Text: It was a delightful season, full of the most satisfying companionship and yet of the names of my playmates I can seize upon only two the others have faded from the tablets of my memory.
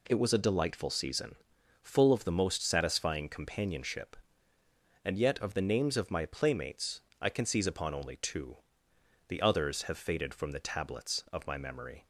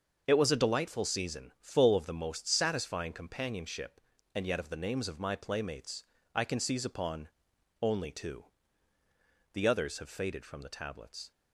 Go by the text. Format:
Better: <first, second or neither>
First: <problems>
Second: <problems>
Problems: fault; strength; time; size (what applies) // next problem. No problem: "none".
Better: first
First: pauses between "playmates" and "I"; slight; at 7.0 s; 0.20 s long // pauses between "two" and "the"; noticeable; at 8.5 s; 0.72 s long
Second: starts louder than the rest; until 1.2 s; 6.5 dB // pauses between "playmates" and "I"; slight; at 6.0 s; 0.28 s long // pauses between "upon" and "only"; noticeable; at 7.2 s; 0.54 s long // pauses between "two" and "the"; at 8.4 s; 1.0 s long // stops before "of my memory"; at 11.3 s